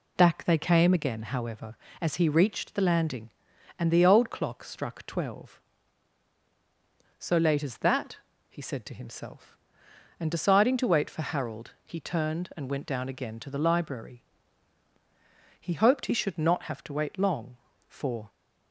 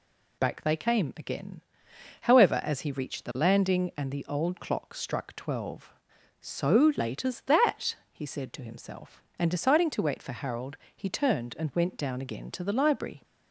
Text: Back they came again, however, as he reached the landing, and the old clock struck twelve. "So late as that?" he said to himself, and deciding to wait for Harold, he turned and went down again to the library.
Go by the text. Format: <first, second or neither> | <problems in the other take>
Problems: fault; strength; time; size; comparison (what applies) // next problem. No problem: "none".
second | goes on to say "He hoped he should not have to wait long for"; strong; from 15.5 s on; 2.7 s long